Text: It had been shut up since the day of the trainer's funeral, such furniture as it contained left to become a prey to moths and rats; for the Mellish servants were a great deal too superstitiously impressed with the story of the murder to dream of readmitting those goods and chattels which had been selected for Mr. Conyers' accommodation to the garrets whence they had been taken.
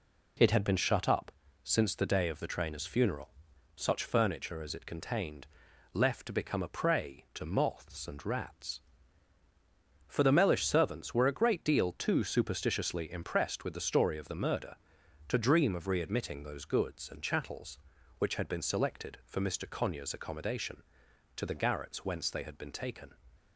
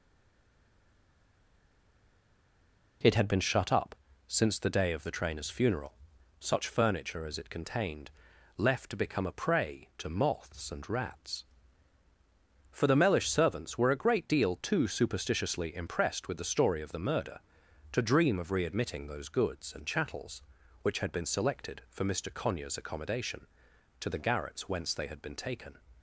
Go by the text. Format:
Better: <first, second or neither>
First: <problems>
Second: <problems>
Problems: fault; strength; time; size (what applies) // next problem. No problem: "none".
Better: first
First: pauses between "up" and "since"; slight; at 1.3 s; 0.32 s long // pauses between "contained" and "left"; noticeable; at 5.4 s; 0.46 s long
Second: stays silent before the first word; strong; until 3.0 s; 3.0 s long // pauses between "up" and "since"; slight; at 3.9 s; 0.32 s long // pauses between "contained" and "left"; noticeable; at 8.1 s; 0.46 s long